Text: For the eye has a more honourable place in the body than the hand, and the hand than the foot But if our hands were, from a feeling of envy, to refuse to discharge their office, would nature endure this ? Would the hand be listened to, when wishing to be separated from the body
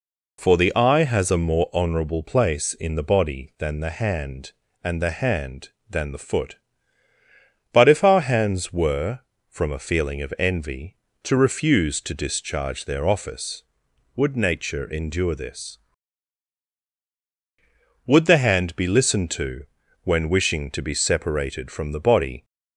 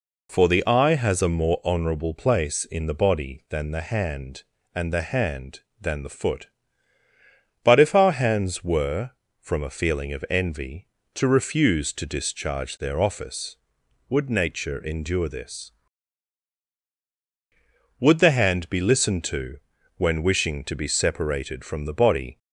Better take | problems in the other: neither | none

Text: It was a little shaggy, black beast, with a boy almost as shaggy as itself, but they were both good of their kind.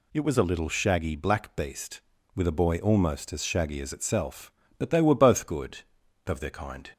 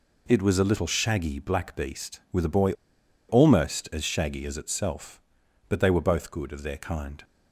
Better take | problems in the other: first | pauses between "boy" and "almost"; noticeable; at 2.7 s; 0.55 s long

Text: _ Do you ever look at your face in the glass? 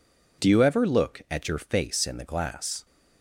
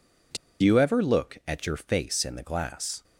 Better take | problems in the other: first | pauses between "Do" and "you"; slight; at 0.3 s; 0.26 s long

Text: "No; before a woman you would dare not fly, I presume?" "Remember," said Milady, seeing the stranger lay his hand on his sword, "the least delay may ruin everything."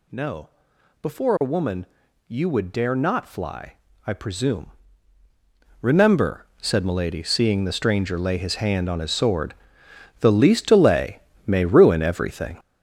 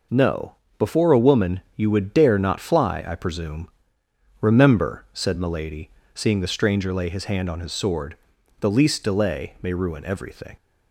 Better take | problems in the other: second | gets louder; strong; throughout; 8 dB // pauses between "woman" and "you"; at 1.8 s; 0.42 s long; slight in the second // pauses between "delay" and "may"; slight; at 11.2 s; 0.26 s long

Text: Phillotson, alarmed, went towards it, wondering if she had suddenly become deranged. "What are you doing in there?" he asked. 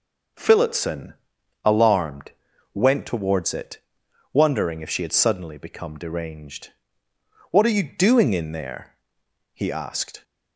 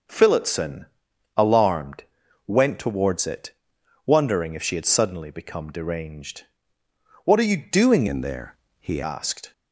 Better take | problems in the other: first | changes voice from "in" to "he"; from 8.0 to 9.0 s; 1.0 s long

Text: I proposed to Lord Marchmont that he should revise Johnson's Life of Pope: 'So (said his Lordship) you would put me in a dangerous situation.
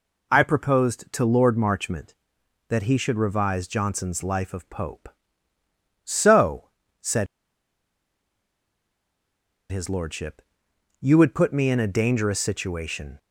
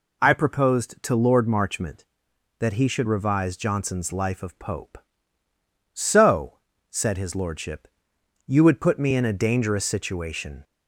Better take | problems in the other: second | pauses between "said" and "his"; strong; at 7.2 s; 2.4 s long

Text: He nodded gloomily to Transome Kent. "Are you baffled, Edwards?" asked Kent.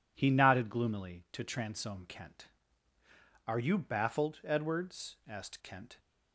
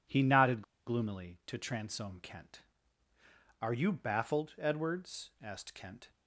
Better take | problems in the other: first | pauses between "nodded" and "gloomily"; slight; at 0.6 s; 0.24 s long

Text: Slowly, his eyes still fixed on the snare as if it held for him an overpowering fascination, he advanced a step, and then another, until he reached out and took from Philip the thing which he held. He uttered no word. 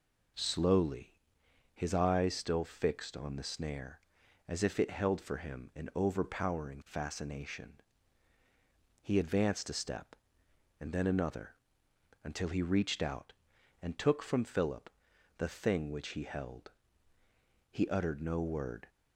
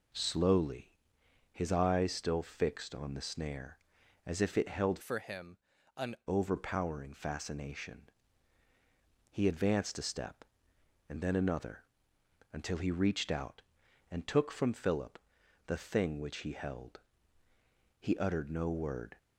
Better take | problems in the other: first | changes voice from "for" to "an"; from 5.0 to 6.1 s; 1.1 s long // pauses between "him" and "an"; at 5.5 s; 0.40 s long // pauses between "Philip" and "the"; noticeable; at 15.1 s; 0.50 s long; noticeable in the first

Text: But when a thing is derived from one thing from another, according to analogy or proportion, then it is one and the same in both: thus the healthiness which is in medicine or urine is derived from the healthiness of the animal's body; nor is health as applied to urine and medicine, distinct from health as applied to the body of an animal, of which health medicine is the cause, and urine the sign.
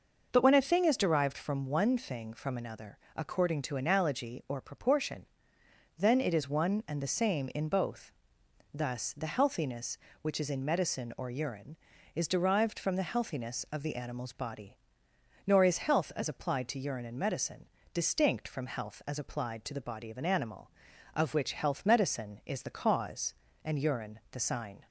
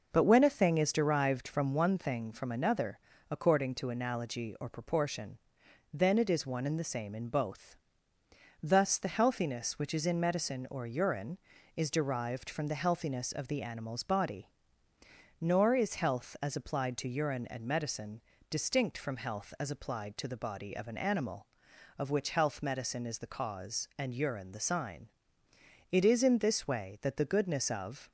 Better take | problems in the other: first | goes on to say "It is in this way that the goodness of"; strong; from 25.9 s on; 2.1 s long

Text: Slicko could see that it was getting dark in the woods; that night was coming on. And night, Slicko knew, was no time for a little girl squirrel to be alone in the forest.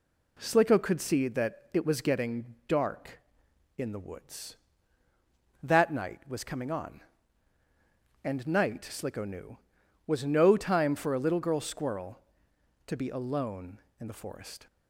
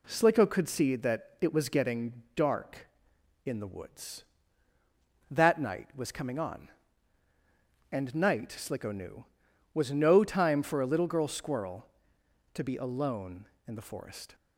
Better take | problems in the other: neither | none

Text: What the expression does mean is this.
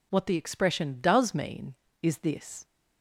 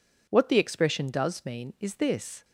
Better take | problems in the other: neither | none

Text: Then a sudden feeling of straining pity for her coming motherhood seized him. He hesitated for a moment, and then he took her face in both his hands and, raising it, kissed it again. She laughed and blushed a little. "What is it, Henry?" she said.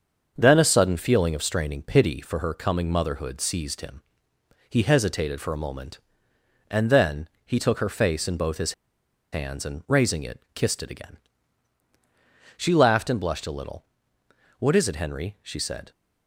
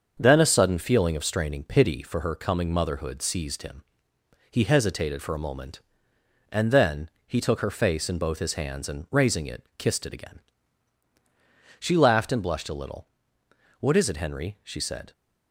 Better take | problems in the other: second | starts louder than the rest; until 1.3 s; 6.5 dB; also in the second // pauses between "then" and "he"; slight; at 7.2 s; 0.20 s long; slight in the second // pauses between "his" and "hands"; noticeable; at 8.7 s; 0.59 s long

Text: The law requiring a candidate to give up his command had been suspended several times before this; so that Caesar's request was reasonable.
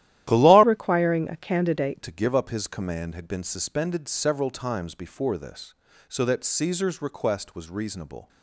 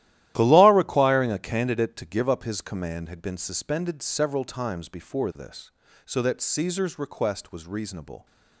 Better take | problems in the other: second | starts louder than the rest; strong; until 1.3 s; 13 dB; strong in the second // changes voice from "requiring" to "candidate"; from 0.6 to 2.0 s; 1.4 s long

